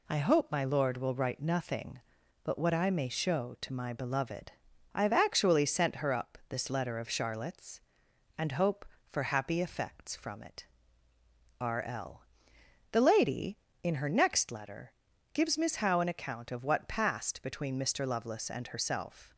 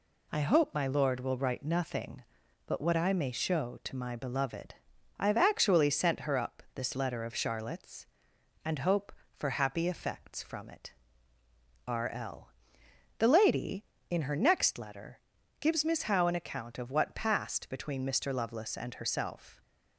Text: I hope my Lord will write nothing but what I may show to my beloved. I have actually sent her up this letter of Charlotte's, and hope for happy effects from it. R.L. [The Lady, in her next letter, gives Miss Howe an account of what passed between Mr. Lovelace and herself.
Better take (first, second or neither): neither